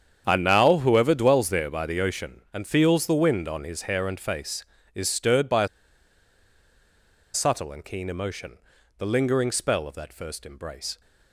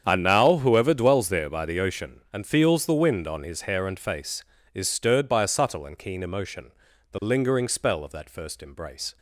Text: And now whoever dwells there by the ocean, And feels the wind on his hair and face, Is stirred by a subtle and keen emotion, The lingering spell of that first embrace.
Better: second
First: starts louder than the rest; strong; until 1.2 s; 8 dB // pauses between "a" and "subtle"; strong; at 5.6 s; 1.6 s long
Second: starts louder than the rest; strong; until 1.0 s; 8 dB

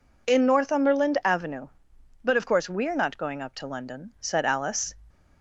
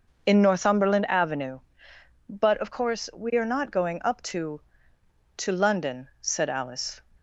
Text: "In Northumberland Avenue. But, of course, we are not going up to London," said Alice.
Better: first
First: none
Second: says "to" twice; at 5.3 s

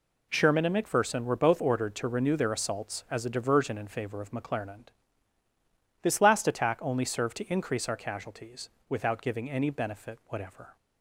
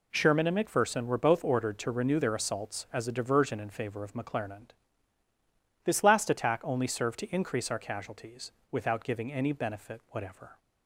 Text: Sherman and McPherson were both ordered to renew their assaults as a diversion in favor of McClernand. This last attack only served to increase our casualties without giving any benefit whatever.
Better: neither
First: pauses between "casualties" and "without"; slight; at 8.6 s; 0.20 s long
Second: pauses between "casualties" and "without"; slight; at 8.5 s; 0.20 s long

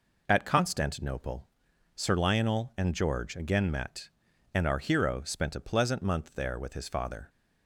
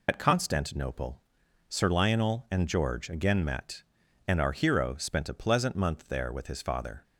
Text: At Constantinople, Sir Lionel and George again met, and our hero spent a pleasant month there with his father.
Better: first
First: none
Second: loses the start of "At"; at 0.0 s; 80 ms

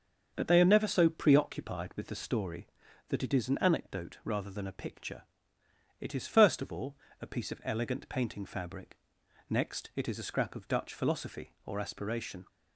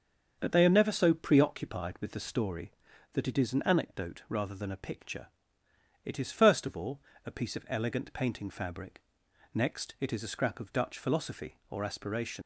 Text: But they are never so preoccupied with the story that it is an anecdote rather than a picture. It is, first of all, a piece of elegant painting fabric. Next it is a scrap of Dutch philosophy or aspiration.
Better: first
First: starts louder than the rest; until 1.3 s; 6.5 dB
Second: starts louder than the rest; until 1.4 s; 6.5 dB // leaves "aspiration" unfinished; at 12.4 s; 100 ms

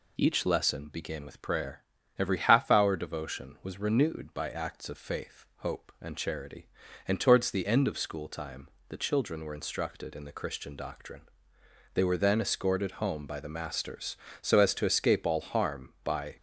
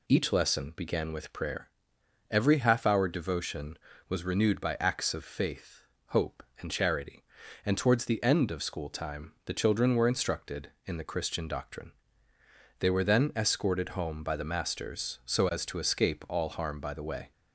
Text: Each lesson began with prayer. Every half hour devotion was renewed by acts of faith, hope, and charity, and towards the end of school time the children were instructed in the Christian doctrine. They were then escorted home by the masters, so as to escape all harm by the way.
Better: second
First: pauses between "time" and "the"; slight; at 8.6 s; 0.22 s long // stops before "the way"; at 16.3 s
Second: none

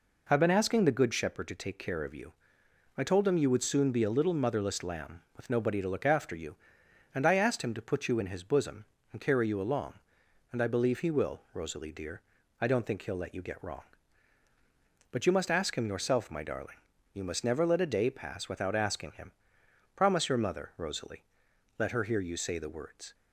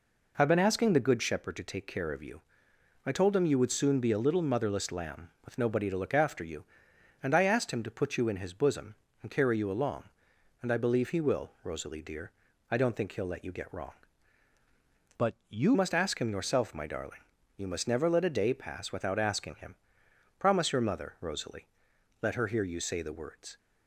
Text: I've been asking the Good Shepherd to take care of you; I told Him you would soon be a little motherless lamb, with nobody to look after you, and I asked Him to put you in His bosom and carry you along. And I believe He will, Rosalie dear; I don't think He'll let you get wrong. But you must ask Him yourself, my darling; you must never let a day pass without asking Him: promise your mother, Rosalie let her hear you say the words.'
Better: first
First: pauses between "Rosalie" and "let"; noticeable; at 21.2 s; 0.56 s long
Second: changes voice from "But" to "you"; from 15.1 to 15.7 s; 0.6 s long // pauses between "Rosalie" and "let"; noticeable; at 21.6 s; 0.56 s long

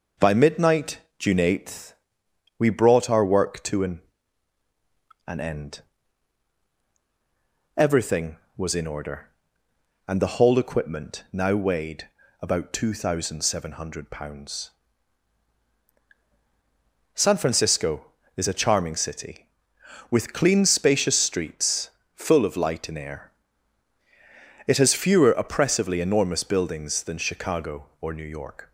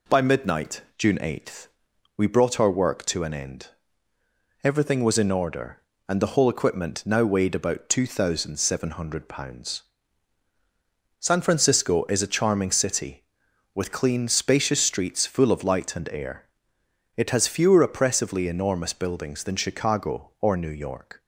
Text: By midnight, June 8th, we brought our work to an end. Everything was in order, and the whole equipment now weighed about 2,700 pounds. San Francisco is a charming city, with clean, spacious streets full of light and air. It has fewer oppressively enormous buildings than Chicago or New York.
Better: second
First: says "an" twice; at 5.2 s // pauses between "weighed" and "about"; slight; at 12.0 s; 0.34 s long // pauses between "streets" and "full"; slight; at 21.9 s; 0.24 s long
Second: none

